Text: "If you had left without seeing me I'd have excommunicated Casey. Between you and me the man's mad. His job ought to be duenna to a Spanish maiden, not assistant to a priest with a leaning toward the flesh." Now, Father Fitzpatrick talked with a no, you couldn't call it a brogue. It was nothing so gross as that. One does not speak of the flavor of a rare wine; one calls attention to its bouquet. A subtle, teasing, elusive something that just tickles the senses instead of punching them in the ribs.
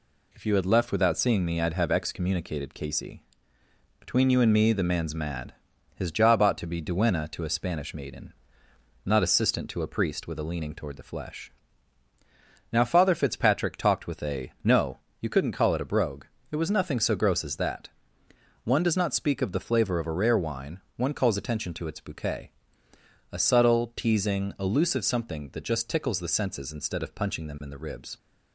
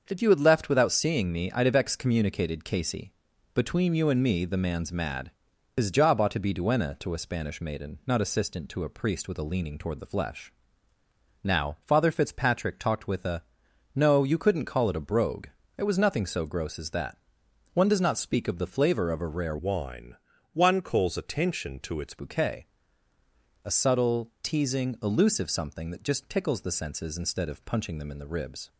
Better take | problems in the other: first | starts louder than the rest; until 1.0 s; 6.5 dB // pauses between "a" and "no"; noticeable; at 13.4 s; 0.54 s long // changes voice from "wine" to "its"; from 19.5 to 22.1 s; 2.6 s long

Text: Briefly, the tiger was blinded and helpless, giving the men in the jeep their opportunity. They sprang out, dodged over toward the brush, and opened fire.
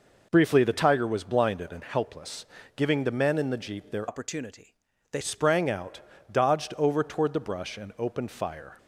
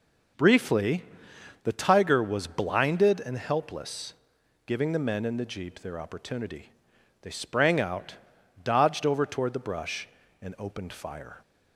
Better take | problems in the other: second | changes voice from "opportunity" to "They"; from 4.0 to 5.2 s; 1.2 s long

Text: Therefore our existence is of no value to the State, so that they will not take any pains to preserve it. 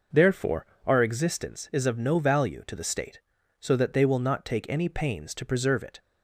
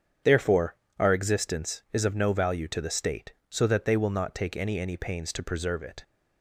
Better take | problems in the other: first | starts louder than the rest; strong; until 1.4 s; 8.5 dB // pauses between "Therefore" and "our"; slight; at 0.7 s; 0.24 s long; slight in the first // says "any" twice; at 4.7 s

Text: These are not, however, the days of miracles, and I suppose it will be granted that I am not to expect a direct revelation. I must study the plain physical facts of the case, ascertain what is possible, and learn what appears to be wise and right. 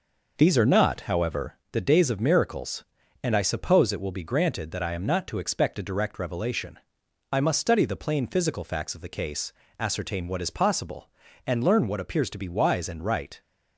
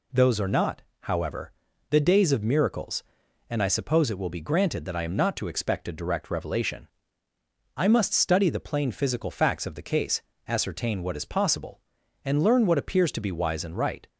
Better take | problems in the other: first | says "Those" for "These"; at 0.1 s

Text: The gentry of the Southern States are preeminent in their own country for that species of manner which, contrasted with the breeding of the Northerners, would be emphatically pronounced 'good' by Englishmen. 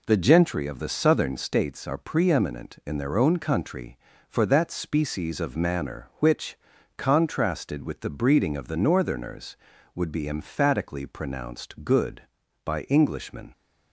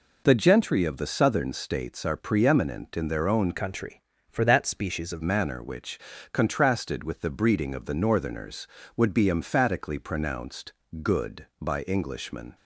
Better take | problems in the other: first | changes voice from "country" to "of"; from 3.5 to 5.2 s; 1.7 s long // pauses between "pronounced" and "good"; slight; at 10.7 s; 0.30 s long

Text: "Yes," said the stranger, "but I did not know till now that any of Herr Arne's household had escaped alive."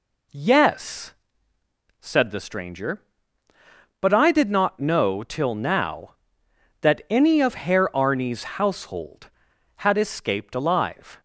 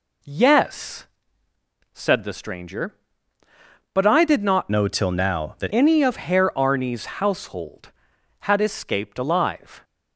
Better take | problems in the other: first | changes voice from "know" to "that"; from 4.6 to 5.7 s; 1.1 s long

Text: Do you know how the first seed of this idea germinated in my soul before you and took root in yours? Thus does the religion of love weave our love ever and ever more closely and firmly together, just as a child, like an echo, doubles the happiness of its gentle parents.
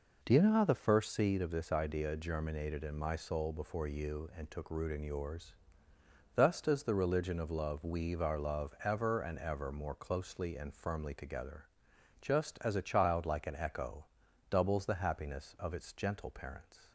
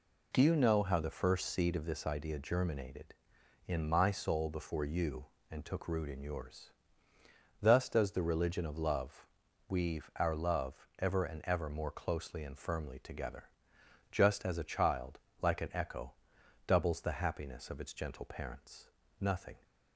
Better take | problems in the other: first | pauses between "love" and "weave"; at 9.2 s; 0.42 s long // goes on to say "Nothing"; slight; from 19.2 s on; 0.42 s long

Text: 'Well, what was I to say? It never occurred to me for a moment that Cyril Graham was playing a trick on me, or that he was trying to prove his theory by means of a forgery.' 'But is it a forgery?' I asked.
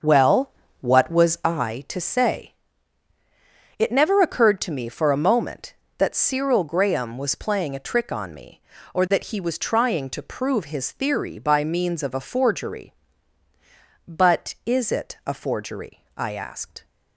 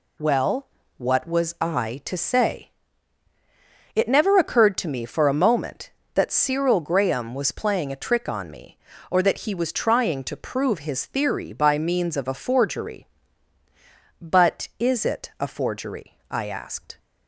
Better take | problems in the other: second | starts louder than the rest; until 1.5 s; 6.5 dB

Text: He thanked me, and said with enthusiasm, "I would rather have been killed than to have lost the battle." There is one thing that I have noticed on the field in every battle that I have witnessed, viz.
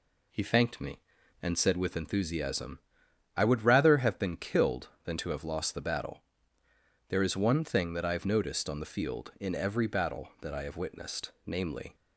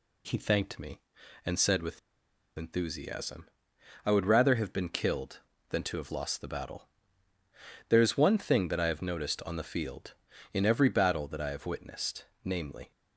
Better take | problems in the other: first | pauses between "with" and "enthusiasm"; noticeable; at 1.9 s; 0.57 s long

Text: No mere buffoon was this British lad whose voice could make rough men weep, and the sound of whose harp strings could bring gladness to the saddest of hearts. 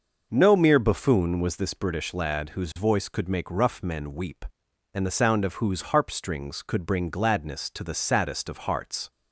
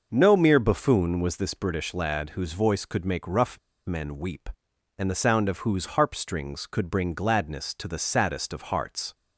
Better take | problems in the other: first | pauses between "rough" and "men"; slight; at 3.5 s; 0.27 s long

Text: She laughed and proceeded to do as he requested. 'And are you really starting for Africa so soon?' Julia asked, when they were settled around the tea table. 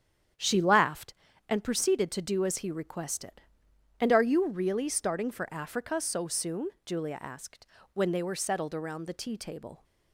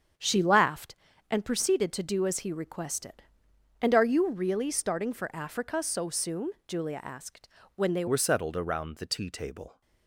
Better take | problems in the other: first | starts louder than the rest; strong; until 1.5 s; 7.5 dB; strong in the first // changes voice at "were"; from 8.0 s on; 1.8 s long

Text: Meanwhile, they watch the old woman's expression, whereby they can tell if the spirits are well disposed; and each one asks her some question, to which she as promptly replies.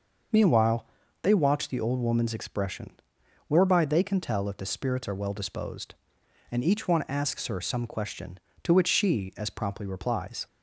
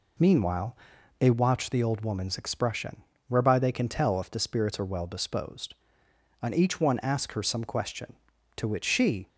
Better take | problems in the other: first | stops before "as promptly replies"; at 9.2 s

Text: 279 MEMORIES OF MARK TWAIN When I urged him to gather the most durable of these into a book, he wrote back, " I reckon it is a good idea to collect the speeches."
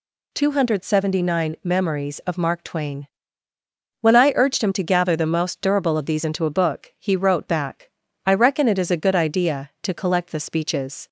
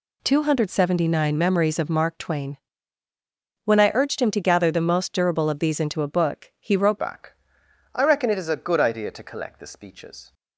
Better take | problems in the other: first | pauses between "TWAIN" and "When"; at 2.5 s; 1.0 s long; noticeable in the first // changes voice at "back"; from 6.9 s on; 3.4 s long

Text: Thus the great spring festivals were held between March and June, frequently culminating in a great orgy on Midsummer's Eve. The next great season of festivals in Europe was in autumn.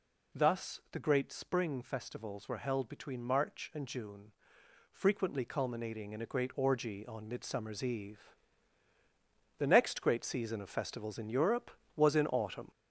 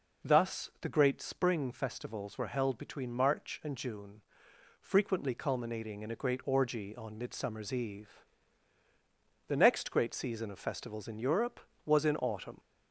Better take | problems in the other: second | gets louder; noticeable; throughout; 5 dB

